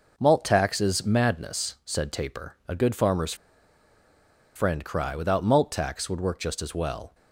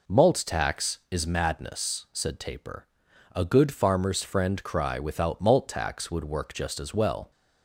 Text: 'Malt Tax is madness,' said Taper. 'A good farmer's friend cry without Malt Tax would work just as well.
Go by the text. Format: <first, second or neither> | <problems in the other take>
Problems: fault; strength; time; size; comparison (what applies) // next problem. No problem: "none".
second | pauses between "farmer's" and "friend"; at 3.3 s; 1.2 s long